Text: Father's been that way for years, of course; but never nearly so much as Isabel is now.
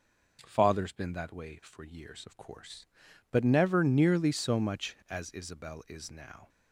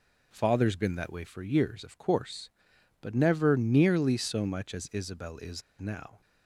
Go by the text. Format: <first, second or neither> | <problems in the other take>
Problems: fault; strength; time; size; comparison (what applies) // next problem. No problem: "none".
first | pauses between "is" and "now"; slight; at 5.6 s; 0.17 s long